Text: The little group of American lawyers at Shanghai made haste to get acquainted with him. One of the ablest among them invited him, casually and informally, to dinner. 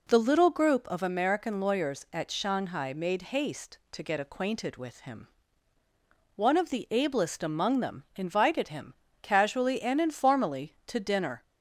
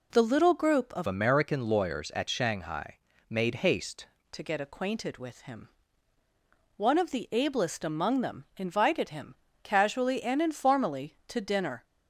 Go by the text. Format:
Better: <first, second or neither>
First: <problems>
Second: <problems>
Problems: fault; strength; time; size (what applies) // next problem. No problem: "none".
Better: first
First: none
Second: changes voice from "American" to "haste"; from 1.0 to 4.0 s; 3.0 s long // pauses between "Shanghai" and "made"; slight; at 2.9 s; 0.30 s long